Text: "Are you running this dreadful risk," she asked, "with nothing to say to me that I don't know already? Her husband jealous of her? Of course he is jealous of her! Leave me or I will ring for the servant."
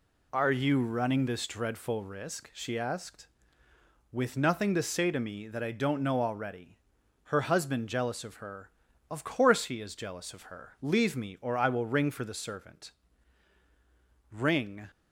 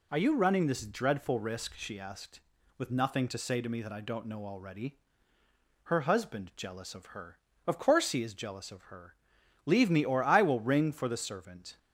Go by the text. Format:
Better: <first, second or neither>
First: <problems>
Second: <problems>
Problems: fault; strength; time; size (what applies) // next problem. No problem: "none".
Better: second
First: goes on to say "Ring"; from 14.3 s on; 0.58 s long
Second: none